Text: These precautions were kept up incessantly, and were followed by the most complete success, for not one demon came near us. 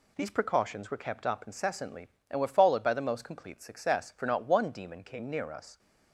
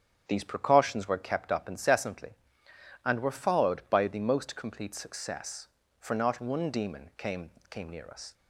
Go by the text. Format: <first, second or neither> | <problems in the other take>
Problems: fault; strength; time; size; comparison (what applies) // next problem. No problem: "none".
first | starts louder than the rest; strong; until 1.2 s; 9 dB // says "came" twice; at 7.6 s